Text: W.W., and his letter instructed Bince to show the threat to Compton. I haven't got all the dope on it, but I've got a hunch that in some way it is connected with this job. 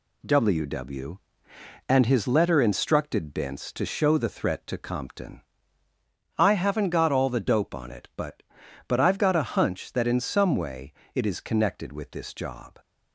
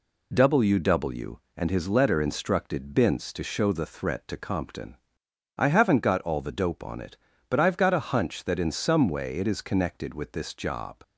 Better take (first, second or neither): second